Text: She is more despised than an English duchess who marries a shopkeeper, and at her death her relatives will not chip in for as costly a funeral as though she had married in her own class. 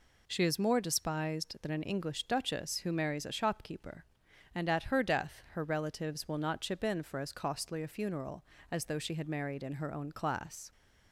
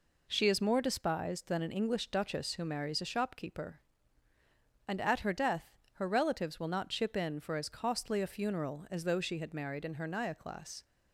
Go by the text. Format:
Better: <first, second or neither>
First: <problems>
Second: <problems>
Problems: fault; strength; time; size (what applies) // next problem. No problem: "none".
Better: first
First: none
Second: pauses between "death" and "her"; slight; at 5.7 s; 0.20 s long // says "naya" for "own"; at 10.0 s